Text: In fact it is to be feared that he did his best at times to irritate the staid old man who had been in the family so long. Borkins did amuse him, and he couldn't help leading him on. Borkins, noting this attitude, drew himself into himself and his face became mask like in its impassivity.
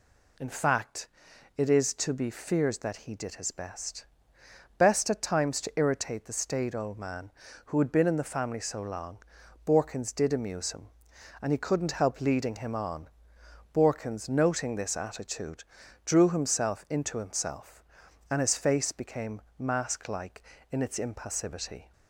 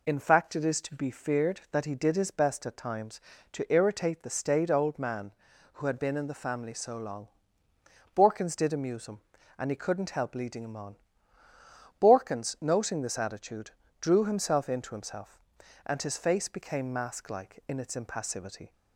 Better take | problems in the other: second | pauses between "fact" and "it"; noticeable; at 1.0 s; 0.50 s long // says "best" twice; at 4.7 s // pauses between "became" and "mask"; slight; at 19.4 s; 0.16 s long

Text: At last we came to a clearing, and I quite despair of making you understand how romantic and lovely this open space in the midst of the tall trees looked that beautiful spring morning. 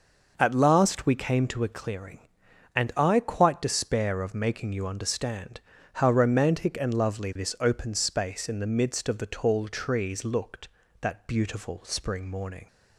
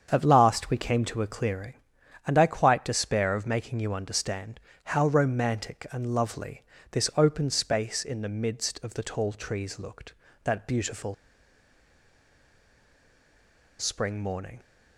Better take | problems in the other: first | starts louder than the rest; strong; until 1.1 s; 7.5 dB; noticeable in the first // pauses between "understand" and "how"; slight; at 4.5 s; 0.26 s long; slight in the first // pauses between "lovely" and "this"; slight; at 6.6 s; 0.28 s long // pauses between "beautiful" and "spring"; strong; at 11.1 s; 2.6 s long

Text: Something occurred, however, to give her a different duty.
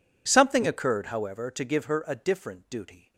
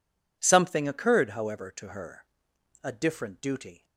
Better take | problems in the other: first | skips "give"; at 1.8 s // pauses between "her" and "a"; noticeable; at 2.2 s; 0.56 s long

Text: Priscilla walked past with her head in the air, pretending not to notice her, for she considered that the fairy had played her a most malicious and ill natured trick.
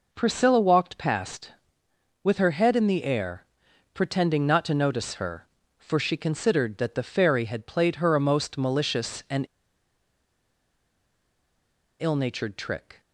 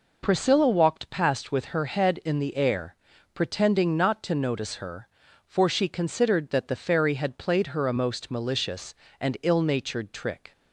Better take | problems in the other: second | pauses between "and" and "ill"; strong; at 9.4 s; 2.5 s long

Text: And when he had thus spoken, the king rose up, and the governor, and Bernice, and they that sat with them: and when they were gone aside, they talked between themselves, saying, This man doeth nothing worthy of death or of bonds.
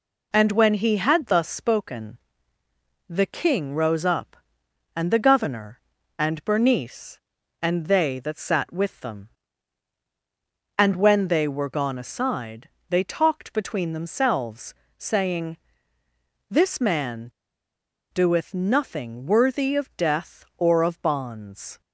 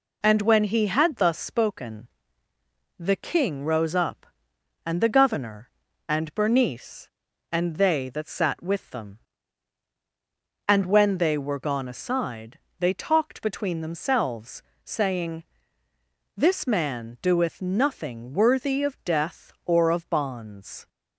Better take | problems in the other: second | pauses between "man" and "doeth"; noticeable; at 17.3 s; 0.82 s long

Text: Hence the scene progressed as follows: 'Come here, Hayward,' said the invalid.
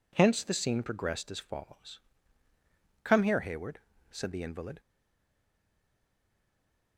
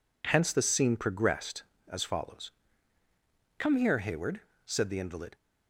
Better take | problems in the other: second | stays silent after the last word; from 4.7 s on; 2.2 s long

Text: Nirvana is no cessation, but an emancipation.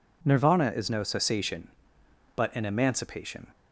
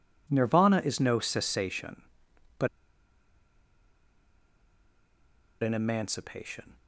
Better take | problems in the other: first | pauses between "but" and "an"; strong; at 2.6 s; 2.9 s long

